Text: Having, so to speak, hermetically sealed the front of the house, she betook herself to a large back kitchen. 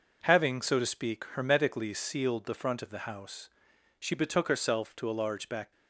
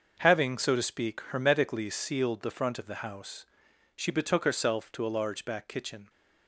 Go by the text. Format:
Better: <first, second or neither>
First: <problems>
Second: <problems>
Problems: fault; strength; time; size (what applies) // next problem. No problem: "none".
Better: second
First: stops before "kitchen"; at 5.7 s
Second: none